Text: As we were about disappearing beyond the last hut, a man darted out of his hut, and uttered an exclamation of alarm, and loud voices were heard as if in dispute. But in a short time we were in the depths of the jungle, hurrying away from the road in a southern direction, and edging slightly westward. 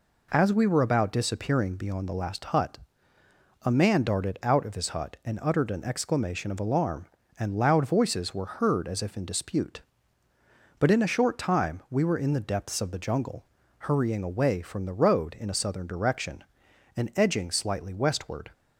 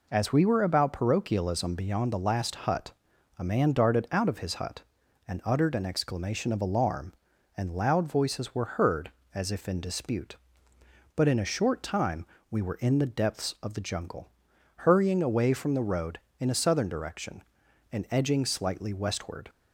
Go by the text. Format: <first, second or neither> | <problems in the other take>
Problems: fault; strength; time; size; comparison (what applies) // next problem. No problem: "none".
first | says "parochialism" for "disappearing"; at 0.9 s // pauses between "time" and "we"; slight; at 12.2 s; 0.24 s long